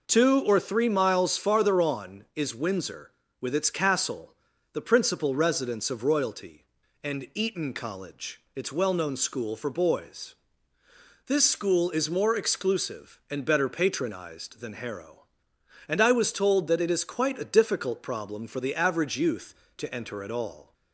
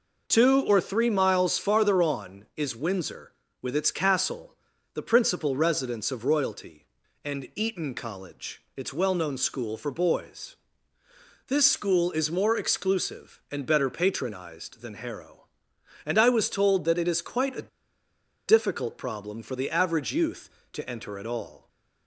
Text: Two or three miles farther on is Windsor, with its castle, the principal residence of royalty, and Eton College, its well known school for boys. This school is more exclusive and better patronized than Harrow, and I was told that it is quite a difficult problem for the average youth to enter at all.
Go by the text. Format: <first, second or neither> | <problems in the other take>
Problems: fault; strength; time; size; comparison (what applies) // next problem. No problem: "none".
first | pauses between "a" and "difficult"; noticeable; at 17.6 s; 0.78 s long